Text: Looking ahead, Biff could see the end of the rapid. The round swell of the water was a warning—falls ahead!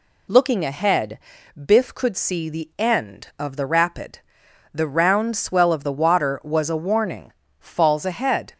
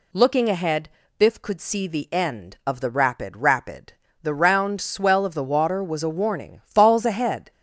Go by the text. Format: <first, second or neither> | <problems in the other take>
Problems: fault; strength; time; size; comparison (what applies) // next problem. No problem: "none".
first | says "rapid" twice; at 3.3 s